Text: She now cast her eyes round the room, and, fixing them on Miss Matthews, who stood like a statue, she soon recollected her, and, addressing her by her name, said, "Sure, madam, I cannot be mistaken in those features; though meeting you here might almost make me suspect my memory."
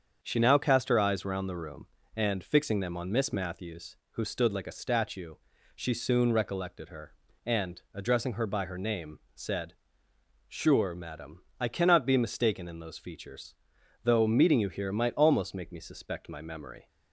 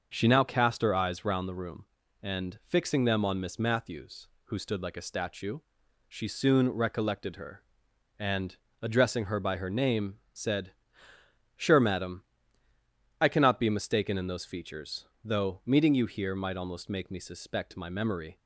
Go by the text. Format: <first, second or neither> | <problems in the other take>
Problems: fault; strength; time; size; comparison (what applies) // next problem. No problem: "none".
neither | starts louder than the rest; the same in both